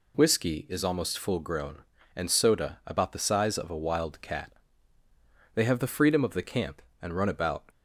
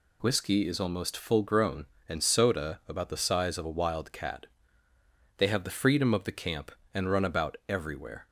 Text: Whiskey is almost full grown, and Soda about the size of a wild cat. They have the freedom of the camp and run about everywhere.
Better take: second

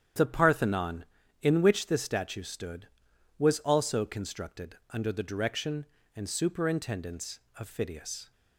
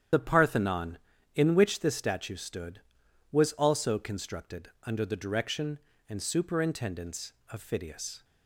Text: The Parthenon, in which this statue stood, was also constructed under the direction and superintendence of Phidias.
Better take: first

